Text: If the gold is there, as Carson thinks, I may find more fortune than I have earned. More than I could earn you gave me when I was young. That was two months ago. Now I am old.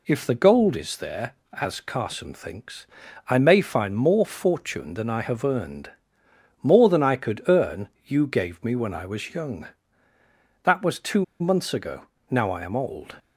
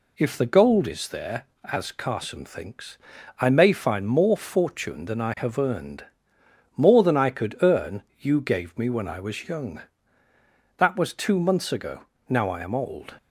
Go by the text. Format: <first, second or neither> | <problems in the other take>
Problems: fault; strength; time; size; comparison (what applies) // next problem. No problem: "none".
second | pauses between "earn" and "you"; slight; at 7.8 s; 0.20 s long; slight in the second // pauses between "two" and "months"; slight; at 11.2 s; 0.15 s long